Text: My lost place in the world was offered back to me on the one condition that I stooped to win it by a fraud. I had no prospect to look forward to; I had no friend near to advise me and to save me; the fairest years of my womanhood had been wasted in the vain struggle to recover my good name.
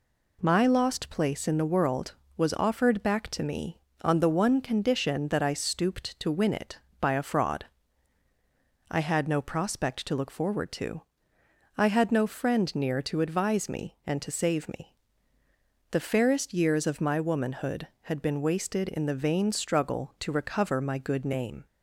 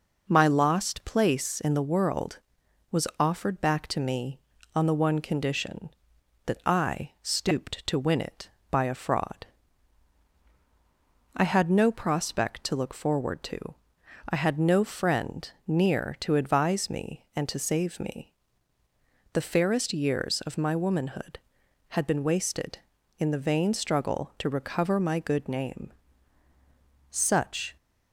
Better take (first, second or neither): first